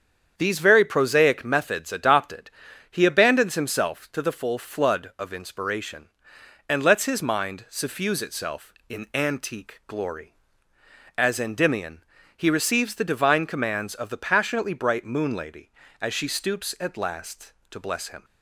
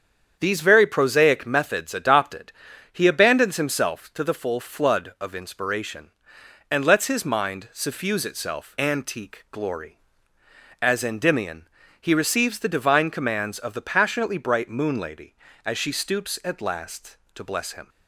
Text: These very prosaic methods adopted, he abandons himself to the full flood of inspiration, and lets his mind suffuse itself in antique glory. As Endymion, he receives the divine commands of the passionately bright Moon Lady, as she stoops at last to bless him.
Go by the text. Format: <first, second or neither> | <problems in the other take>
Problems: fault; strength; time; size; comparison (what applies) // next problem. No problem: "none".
first | starts louder than the rest; strong; until 1.4 s; 7.5 dB; strong in the first // skips "in"; at 8.7 s